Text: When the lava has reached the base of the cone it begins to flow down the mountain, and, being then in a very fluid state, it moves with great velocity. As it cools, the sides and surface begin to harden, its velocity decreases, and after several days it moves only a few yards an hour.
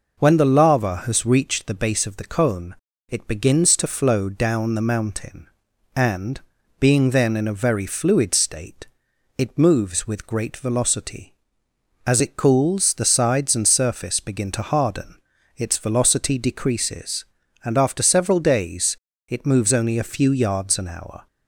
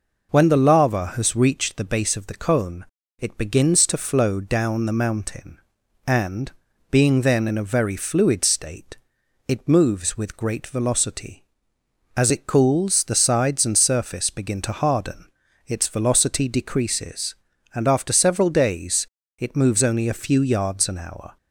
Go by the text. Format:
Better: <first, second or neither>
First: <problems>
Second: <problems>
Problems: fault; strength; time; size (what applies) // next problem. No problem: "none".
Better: neither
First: pauses between "cone" and "it"; slight; at 2.7 s; 0.34 s long // pauses between "days" and "it"; slight; at 18.9 s; 0.32 s long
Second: pauses between "cone" and "it"; slight; at 2.8 s; 0.34 s long // pauses between "days" and "it"; slight; at 19.0 s; 0.32 s long